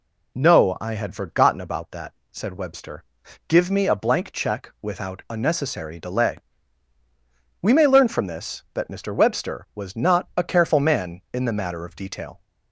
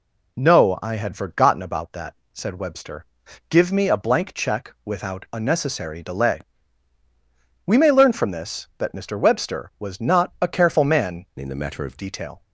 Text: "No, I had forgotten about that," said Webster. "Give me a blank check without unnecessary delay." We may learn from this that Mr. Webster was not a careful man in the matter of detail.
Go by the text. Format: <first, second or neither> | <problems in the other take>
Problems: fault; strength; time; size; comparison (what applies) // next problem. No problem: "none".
first | changes voice from "in" to "of"; from 11.3 to 11.9 s; 0.6 s long